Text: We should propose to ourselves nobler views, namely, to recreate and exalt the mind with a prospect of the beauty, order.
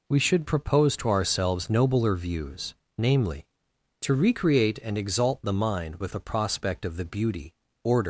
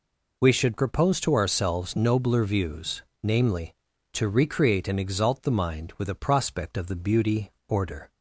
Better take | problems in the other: second | leaves "order" unfinished; at 8.0 s; 125 ms

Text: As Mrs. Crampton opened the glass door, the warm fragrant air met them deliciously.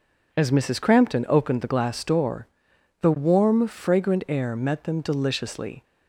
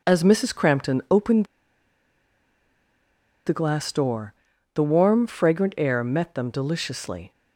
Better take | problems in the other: first | pauses between "opened" and "the"; strong; at 1.4 s; 2.0 s long

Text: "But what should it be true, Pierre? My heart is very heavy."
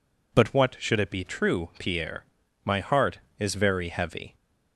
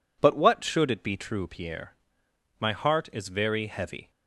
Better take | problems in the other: neither | none

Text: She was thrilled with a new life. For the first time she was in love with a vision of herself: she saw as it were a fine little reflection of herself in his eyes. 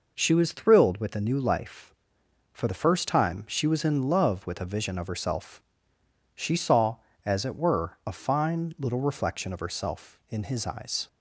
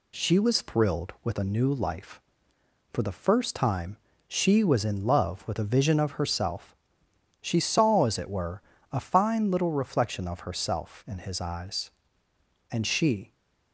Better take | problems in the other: first | pauses between "time" and "she"; slight; at 3.9 s; 0.32 s long // pauses between "were" and "a"; slight; at 8.6 s; 0.32 s long // goes on to say "And she"; noticeable; from 12.7 s on; 0.62 s long

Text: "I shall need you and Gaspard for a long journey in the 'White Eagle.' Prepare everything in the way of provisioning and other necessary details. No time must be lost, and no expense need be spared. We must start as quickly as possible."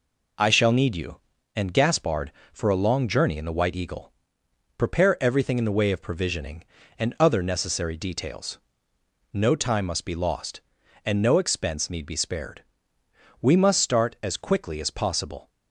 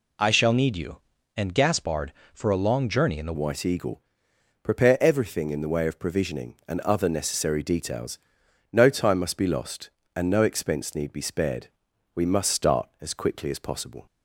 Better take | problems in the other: first | changes voice at "White"; from 3.3 s on; 10.7 s long

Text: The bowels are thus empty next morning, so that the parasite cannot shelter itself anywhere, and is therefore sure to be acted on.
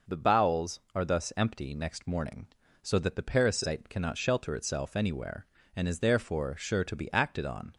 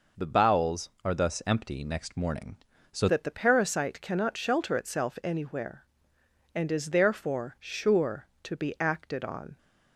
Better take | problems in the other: first | changes voice at "that"; from 3.0 s on; 6.5 s long

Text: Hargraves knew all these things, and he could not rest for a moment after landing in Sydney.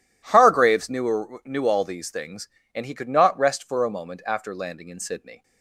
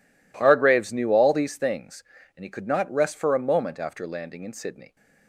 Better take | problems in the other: second | says "knew" twice; at 1.4 s

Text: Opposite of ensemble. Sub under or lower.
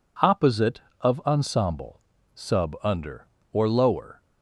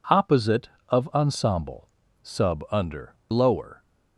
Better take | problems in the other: first | skips "or"; at 3.2 s

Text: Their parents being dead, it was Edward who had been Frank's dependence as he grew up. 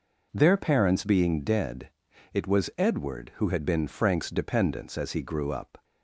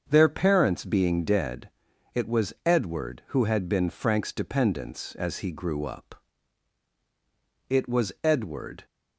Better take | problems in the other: first | starts louder than the rest; until 1.0 s; 7 dB // goes on to say "It was Edward"; noticeable; from 7.6 s on; 1.1 s long

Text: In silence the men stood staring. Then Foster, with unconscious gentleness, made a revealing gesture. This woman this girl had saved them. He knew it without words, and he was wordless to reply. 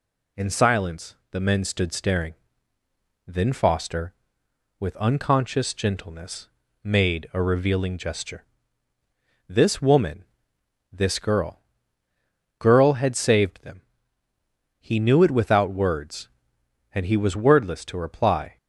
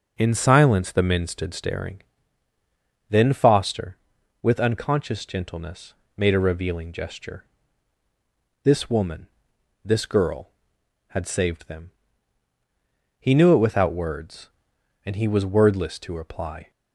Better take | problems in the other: second | pauses between "silence" and "the"; slight; at 1.1 s; 0.16 s long // pauses between "woman" and "this"; noticeable; at 10.2 s; 0.68 s long; noticeable in the second // says "girl" twice; at 12.5 s

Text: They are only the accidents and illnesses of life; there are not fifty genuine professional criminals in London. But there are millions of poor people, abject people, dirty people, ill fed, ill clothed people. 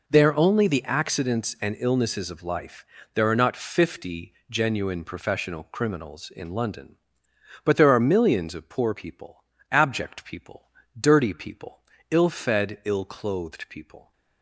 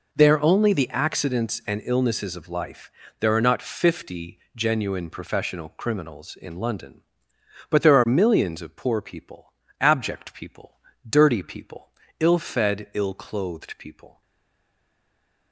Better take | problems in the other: first | stays silent after the last word; noticeable; from 14.2 s on; 1.3 s long

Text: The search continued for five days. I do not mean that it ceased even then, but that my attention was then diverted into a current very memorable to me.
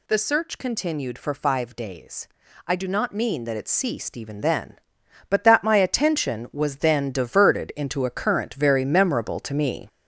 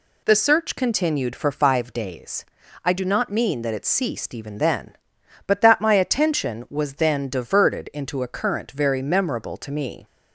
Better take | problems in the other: second | gets louder; noticeable; throughout; 6 dB

